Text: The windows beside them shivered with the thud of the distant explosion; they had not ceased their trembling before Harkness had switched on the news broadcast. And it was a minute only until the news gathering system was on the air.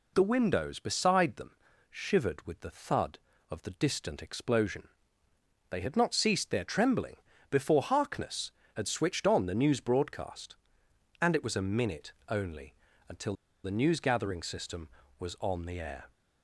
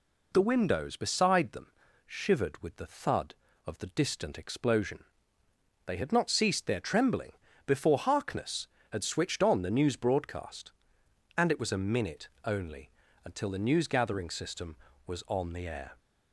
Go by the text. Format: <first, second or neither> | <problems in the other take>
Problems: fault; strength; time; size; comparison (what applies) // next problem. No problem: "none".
second | pauses between "them" and "shivered"; slight; at 1.5 s; 0.34 s long; slight in the second // pauses between "trembling" and "before"; slight; at 7.1 s; 0.32 s long; slight in the second // pauses between "minute" and "only"; slight; at 12.1 s; 0.16 s long; slight in the second // pauses between "only" and "until"; slight; at 12.7 s; 0.34 s long; slight in the second // pauses between "until" and "the"; slight; at 13.3 s; 0.31 s long